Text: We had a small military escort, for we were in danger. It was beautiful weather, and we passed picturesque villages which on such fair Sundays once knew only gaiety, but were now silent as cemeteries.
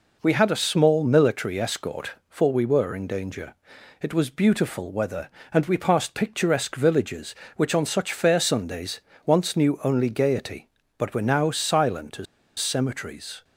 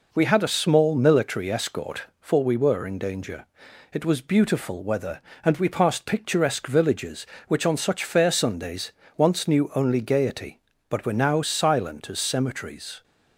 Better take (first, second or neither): second